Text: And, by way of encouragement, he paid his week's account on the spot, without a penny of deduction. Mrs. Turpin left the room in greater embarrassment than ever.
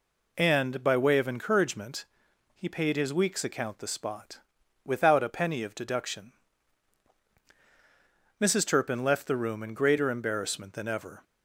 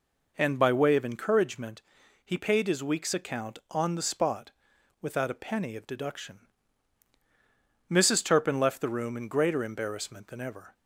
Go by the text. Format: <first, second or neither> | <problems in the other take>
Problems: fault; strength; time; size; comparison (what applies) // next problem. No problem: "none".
second | skips "on"; at 3.8 s